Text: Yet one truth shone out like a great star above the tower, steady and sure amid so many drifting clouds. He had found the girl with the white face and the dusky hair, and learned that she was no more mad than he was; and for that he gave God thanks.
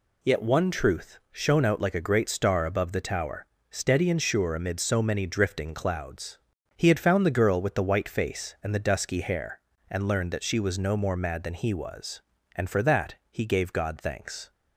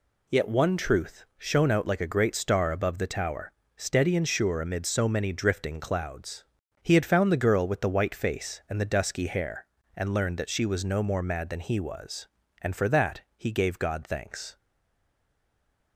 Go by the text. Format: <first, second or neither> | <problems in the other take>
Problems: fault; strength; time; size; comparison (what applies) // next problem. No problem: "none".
first | pauses between "that" and "he"; slight; at 13.2 s; 0.16 s long; slight in the first // stays silent after the last word; noticeable; from 14.5 s on; 1.4 s long